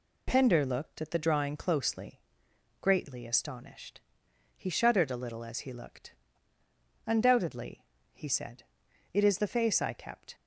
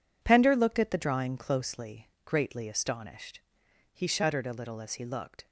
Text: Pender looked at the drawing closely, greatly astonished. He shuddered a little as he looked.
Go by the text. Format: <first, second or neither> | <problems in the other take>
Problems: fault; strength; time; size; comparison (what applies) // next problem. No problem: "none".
second | goes on to say "Undoubtedly he said it is the face I kept"; strong; from 7.0 s on; 3.2 s long